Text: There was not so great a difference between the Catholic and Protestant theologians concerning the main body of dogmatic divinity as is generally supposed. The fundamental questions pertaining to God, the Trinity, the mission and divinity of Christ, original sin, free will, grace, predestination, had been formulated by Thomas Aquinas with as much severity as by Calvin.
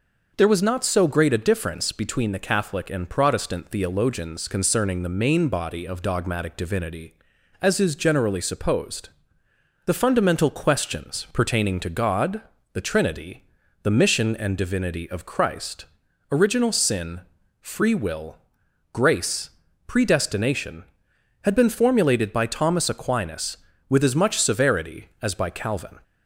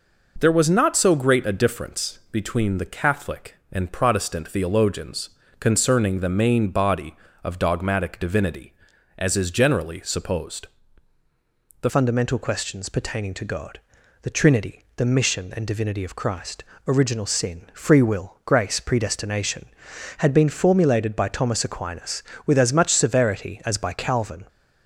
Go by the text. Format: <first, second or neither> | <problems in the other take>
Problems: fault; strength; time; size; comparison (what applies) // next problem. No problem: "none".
first | pauses between "theologians" and "concerning"; slight; at 5.3 s; 0.28 s long // changes voice at "fundamental"; from 11.8 s on; 12.6 s long